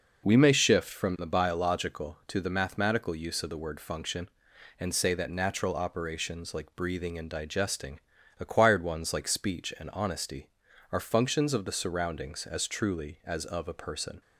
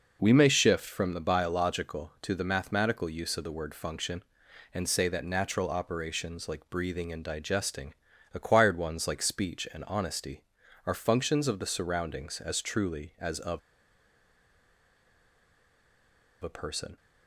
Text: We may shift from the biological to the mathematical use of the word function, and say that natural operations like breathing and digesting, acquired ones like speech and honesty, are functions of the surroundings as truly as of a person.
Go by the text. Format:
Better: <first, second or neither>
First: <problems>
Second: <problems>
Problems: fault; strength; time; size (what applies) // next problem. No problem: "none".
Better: first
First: none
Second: pauses between "of" and "a"; strong; at 13.5 s; 2.8 s long